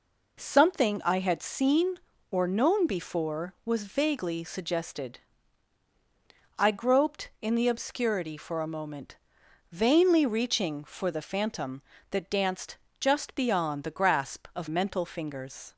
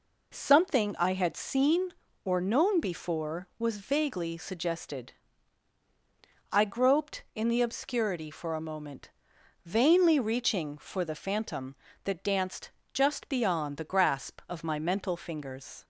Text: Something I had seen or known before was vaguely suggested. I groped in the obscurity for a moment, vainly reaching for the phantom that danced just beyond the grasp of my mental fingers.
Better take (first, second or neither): second